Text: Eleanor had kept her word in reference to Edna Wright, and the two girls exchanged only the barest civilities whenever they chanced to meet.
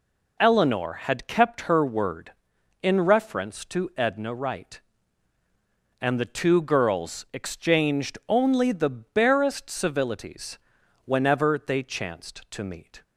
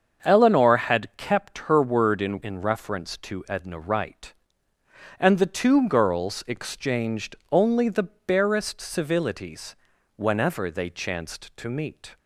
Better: first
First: pauses between "civilities" and "whenever"; noticeable; at 10.5 s; 0.46 s long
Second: starts louder than the rest; until 1.3 s; 7 dB // says "in" twice; at 2.4 s // pauses between "exchanged" and "only"; slight; at 7.3 s; 0.16 s long // pauses between "the" and "barest"; slight; at 8.0 s; 0.18 s long // pauses between "civilities" and "whenever"; at 9.7 s; 0.42 s long

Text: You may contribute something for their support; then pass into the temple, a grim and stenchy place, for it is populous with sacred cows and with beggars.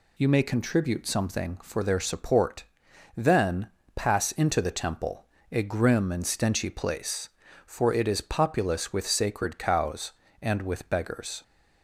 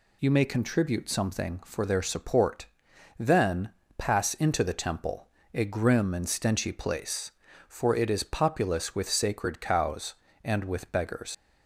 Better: first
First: pauses between "then" and "pass"; slight; at 3.6 s; 0.26 s long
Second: pauses between "then" and "pass"; slight; at 3.7 s; 0.26 s long // leaves "beggars" unfinished; at 11.3 s; 100 ms

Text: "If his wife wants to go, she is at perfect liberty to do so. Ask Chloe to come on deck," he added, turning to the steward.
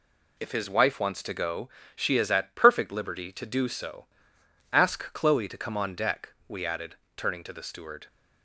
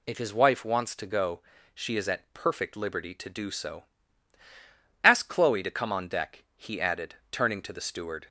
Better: second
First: says "we" for "he"; at 6.4 s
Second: none

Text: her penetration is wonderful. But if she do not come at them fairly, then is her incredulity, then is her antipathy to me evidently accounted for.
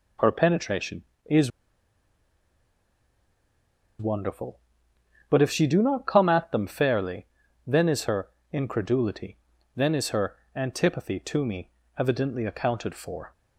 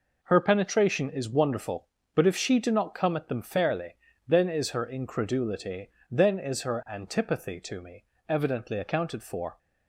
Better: second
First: pauses between "is" and "wonderful"; strong; at 1.4 s; 2.4 s long // pauses between "her" and "incredulity"; slight; at 8.2 s; 0.24 s long // pauses between "her" and "antipathy"; slight; at 10.3 s; 0.18 s long // pauses between "me" and "evidently"; slight; at 11.7 s; 0.28 s long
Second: pauses between "me" and "evidently"; slight; at 8.0 s; 0.24 s long

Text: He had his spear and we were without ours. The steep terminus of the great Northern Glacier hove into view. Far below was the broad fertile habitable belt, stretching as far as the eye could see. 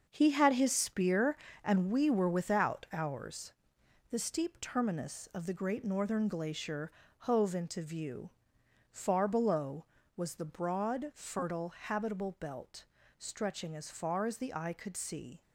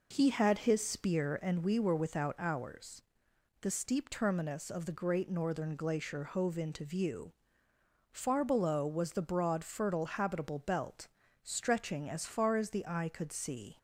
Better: second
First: gets quieter; strong; throughout; 8.5 dB // pauses between "Glacier" and "hove"; slight; at 6.9 s; 0.28 s long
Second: none

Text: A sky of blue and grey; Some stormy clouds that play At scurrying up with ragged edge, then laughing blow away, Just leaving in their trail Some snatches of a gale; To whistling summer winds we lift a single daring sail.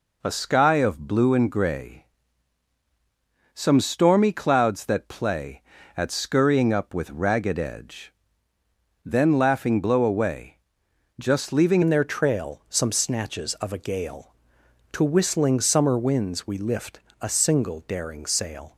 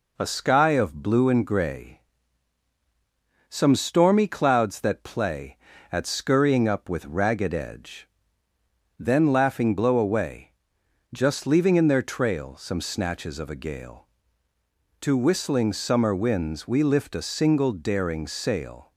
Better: second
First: changes voice at "in"; from 11.8 s on; 6.9 s long // pauses between "lift" and "a"; slight; at 16.9 s; 0.22 s long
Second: none

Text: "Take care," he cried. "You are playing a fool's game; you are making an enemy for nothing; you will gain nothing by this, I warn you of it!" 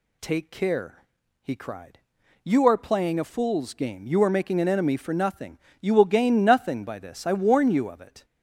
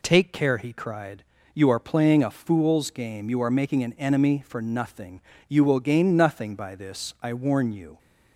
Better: first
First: none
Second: stops before "of it"; at 7.9 s

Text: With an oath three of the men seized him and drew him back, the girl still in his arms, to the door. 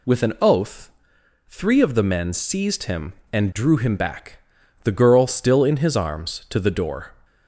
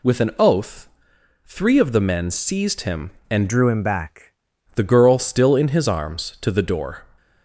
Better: first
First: pauses between "oath" and "three"; noticeable; at 0.8 s; 0.58 s long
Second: pauses between "oath" and "three"; noticeable; at 0.8 s; 0.58 s long // changes voice from "drew" to "back"; from 3.4 to 4.3 s; 0.9 s long

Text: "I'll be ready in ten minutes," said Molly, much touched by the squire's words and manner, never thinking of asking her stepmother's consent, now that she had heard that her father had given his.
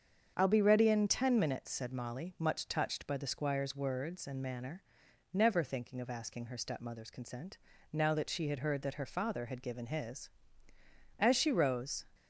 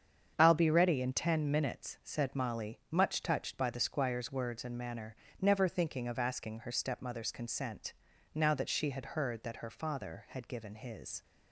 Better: second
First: starts louder than the rest; strong; until 1.3 s; 7 dB // goes on to say "As she rose"; noticeable; from 11.1 s on; 0.86 s long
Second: starts louder than the rest; strong; until 1.3 s; 7.5 dB

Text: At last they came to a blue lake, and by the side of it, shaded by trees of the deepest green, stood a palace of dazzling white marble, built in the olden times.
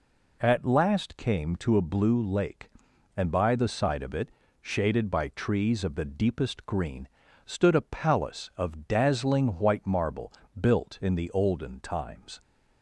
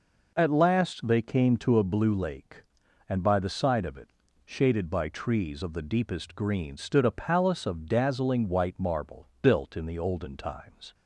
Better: second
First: skips "they"; at 1.1 s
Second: none

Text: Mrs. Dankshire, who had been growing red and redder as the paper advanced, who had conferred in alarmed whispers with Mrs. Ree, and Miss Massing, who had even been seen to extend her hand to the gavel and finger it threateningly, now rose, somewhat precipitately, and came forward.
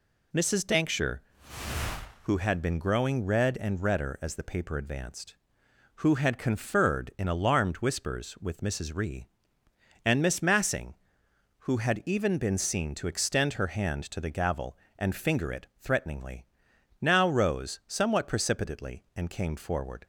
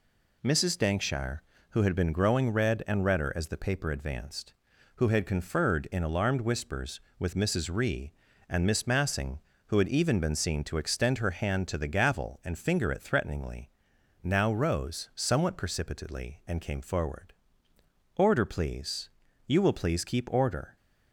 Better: first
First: none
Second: goes on to say "Order please You will please keep order"; strong; from 18.1 s on; 2.6 s long

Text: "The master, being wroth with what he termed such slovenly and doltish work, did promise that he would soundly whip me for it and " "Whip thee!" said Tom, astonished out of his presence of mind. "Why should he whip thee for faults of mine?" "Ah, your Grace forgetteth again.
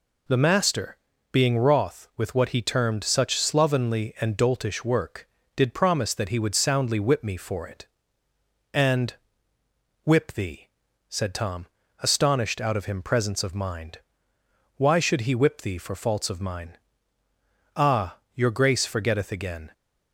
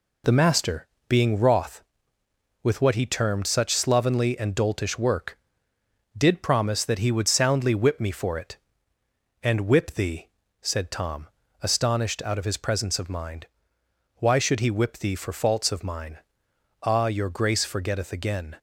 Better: second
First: says "him" for "his"; at 12.8 s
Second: none

